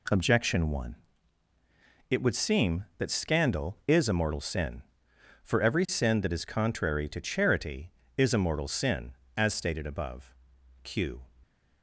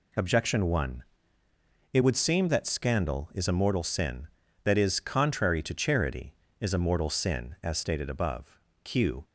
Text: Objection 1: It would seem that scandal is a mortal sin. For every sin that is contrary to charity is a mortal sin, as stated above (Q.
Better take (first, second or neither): first